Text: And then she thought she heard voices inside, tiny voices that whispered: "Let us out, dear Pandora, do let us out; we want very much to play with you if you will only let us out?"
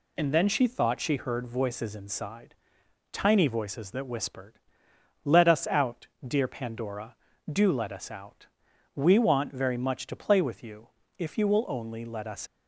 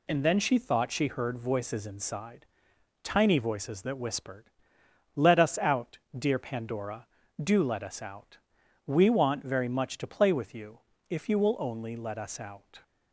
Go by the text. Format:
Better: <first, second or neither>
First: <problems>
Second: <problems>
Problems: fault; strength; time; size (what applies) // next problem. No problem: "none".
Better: second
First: pauses between "you" and "if"; slight; at 10.8 s; 0.30 s long // stops before "out"; at 12.4 s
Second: pauses between "you" and "if"; slight; at 10.7 s; 0.30 s long